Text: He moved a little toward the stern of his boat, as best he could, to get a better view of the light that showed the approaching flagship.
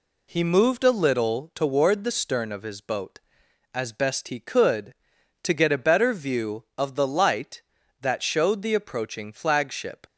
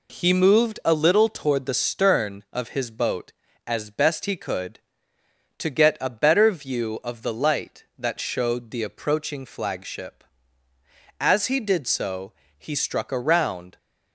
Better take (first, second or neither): first